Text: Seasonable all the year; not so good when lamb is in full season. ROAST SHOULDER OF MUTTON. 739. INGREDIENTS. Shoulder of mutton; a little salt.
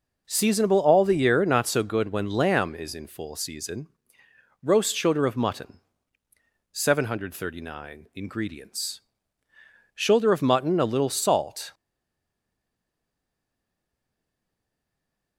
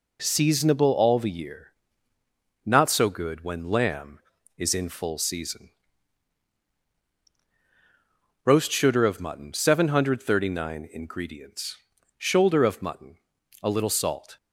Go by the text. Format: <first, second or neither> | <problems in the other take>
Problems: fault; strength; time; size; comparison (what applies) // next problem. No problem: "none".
second | stays silent after the last word; strong; from 11.7 s on; 3.6 s long